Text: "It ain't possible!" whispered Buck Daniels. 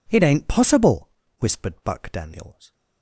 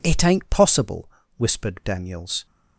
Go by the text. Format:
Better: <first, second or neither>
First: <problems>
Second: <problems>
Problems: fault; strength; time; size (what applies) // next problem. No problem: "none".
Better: first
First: none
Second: skips "Buck"; at 1.8 s